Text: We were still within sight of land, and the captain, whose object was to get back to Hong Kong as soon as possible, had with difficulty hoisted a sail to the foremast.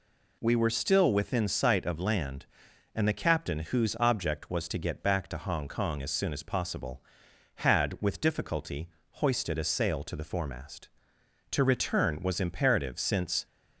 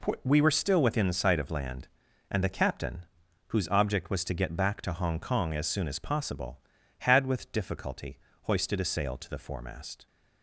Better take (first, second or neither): second